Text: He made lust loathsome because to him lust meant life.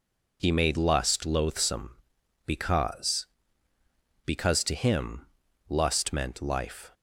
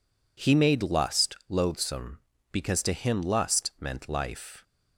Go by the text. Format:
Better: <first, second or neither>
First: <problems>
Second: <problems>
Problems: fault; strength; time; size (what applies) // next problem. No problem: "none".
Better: second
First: says "because" twice; at 4.2 s // pauses between "him" and "lust"; at 5.2 s; 0.42 s long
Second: none